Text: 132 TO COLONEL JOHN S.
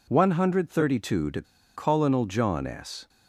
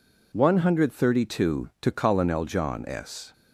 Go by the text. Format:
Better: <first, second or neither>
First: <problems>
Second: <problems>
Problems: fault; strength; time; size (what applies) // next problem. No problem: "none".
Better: second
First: pauses between "TO" and "COLONEL"; slight; at 1.4 s; 0.33 s long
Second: none